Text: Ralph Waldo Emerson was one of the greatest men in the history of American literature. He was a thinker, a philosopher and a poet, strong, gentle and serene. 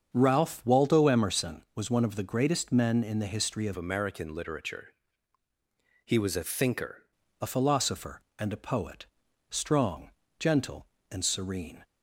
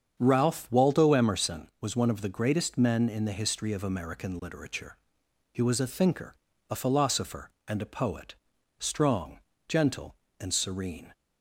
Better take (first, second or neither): second